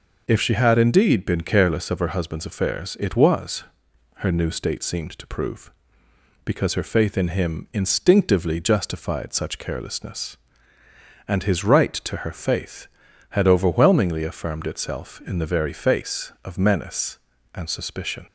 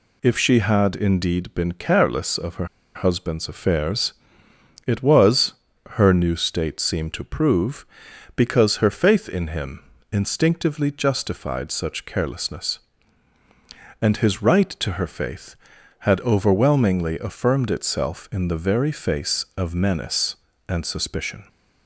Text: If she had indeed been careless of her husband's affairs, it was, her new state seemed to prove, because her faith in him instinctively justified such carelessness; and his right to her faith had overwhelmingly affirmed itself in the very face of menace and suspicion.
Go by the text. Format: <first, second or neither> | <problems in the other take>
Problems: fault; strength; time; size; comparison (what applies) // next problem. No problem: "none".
first | pauses between "her" and "husband's"; slight; at 2.6 s; 0.29 s long // pauses between "him" and "instinctively"; slight; at 9.8 s; 0.28 s long